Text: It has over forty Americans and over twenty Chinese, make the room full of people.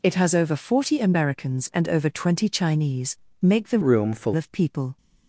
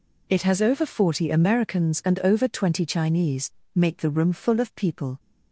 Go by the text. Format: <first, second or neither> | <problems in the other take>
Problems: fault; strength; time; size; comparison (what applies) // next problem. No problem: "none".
second | changes voice from "room" to "full"; from 3.8 to 4.3 s; 0.5 s long